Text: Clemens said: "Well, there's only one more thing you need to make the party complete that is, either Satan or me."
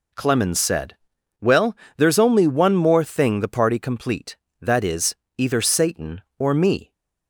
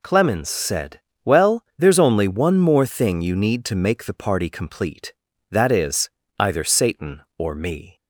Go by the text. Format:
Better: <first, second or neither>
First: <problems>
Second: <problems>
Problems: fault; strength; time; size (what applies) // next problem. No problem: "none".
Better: second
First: skips "you need to make"; at 3.4 s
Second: none